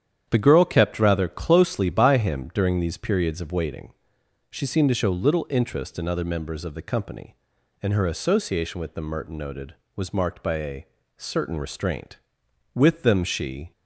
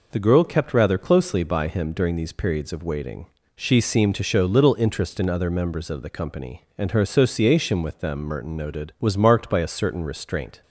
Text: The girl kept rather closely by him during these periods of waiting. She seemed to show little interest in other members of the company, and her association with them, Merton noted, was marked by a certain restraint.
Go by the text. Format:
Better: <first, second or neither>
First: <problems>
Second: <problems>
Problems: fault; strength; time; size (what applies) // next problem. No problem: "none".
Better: second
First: starts louder than the rest; strong; until 1.3 s; 9 dB // pauses between "a" and "certain"; slight; at 10.8 s; 0.30 s long // goes on to say "With them she"; noticeable; from 12.7 s on; 0.98 s long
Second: none